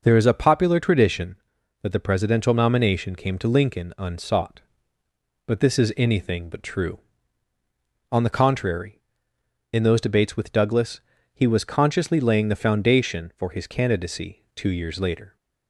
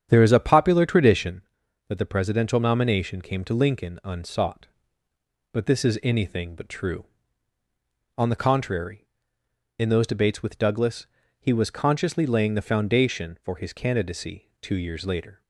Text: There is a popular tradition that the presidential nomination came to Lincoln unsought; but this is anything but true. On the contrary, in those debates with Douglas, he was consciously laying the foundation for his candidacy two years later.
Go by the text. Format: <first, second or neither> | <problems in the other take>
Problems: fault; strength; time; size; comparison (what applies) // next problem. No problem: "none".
first | starts louder than the rest; strong; until 1.4 s; 9 dB